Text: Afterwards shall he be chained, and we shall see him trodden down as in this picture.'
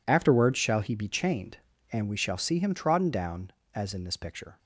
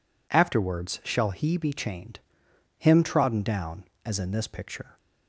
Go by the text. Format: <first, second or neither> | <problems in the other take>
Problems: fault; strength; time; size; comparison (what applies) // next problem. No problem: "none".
first | skips "and we shall see"; at 2.4 s